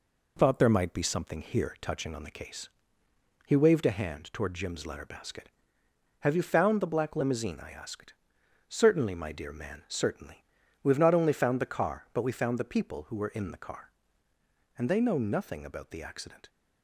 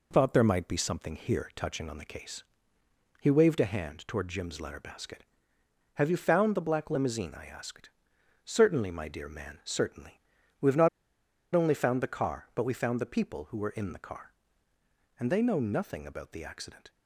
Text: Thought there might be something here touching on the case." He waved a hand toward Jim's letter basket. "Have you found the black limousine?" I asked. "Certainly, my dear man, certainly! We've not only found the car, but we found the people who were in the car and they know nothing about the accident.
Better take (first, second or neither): first